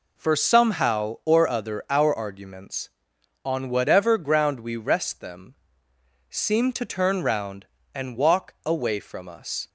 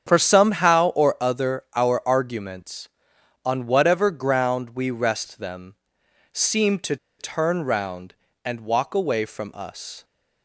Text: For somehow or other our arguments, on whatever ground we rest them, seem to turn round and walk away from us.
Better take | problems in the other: first | starts louder than the rest; strong; until 1.1 s; 8.5 dB // pauses between "to" and "turn"; slight; at 6.9 s; 0.23 s long

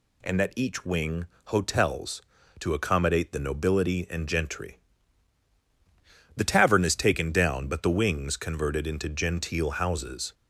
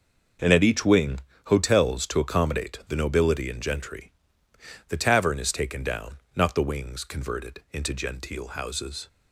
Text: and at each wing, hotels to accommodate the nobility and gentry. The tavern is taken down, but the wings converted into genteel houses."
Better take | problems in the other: first | says "not" for "but"; at 6.3 s

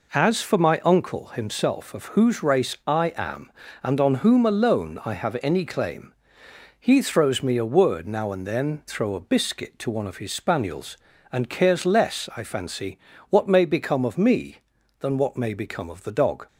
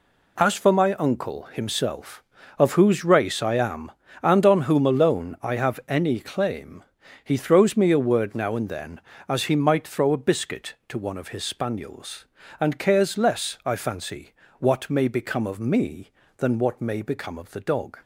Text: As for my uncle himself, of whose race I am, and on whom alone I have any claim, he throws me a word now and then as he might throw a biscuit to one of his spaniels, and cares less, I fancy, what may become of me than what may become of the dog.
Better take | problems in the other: second | skips "as he might"; at 8.8 s

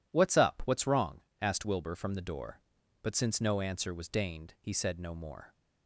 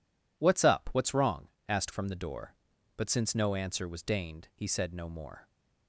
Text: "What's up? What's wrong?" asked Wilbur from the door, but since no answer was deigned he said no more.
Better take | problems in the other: first | skips "Wilbur"; at 1.9 s

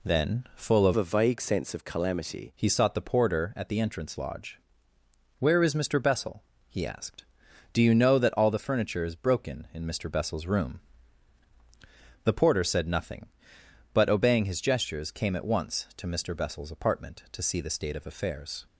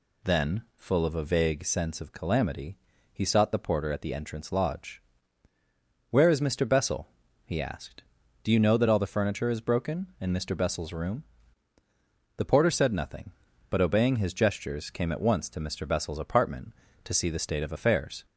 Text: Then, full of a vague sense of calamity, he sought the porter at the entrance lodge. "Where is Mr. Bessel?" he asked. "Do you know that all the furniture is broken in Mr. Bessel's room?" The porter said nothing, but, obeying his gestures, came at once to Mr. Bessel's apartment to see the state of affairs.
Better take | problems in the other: second | changes voice from "a" to "calamity"; from 0.9 to 2.5 s; 1.6 s long

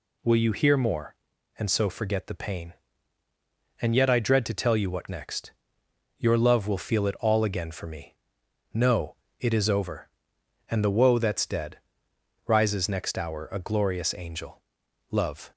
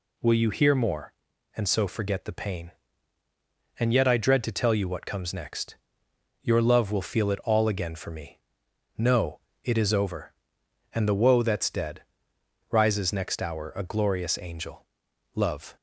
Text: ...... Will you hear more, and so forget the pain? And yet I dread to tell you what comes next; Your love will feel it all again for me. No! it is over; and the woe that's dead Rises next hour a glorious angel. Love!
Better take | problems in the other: second | skips "comes"; at 5.0 s // pauses between "dead" and "Rises"; noticeable; at 11.7 s; 0.72 s long; noticeable in the second

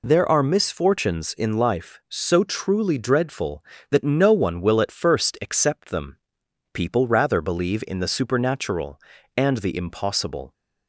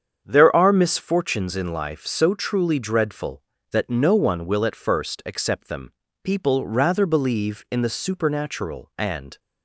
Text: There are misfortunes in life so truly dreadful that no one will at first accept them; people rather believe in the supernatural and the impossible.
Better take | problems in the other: first | starts louder than the rest; strong; until 1.2 s; 8 dB // stops before "the impossible"; at 9.3 s

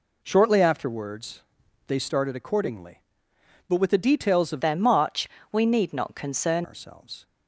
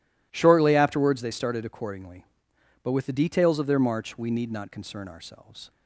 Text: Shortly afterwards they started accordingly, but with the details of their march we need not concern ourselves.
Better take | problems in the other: second | pauses between "afterwards" and "they"; noticeable; at 1.4 s; 0.46 s long // changes voice from "their" to "concern"; from 4.6 to 6.6 s; 2.0 s long // pauses between "march" and "we"; slight; at 5.2 s; 0.24 s long

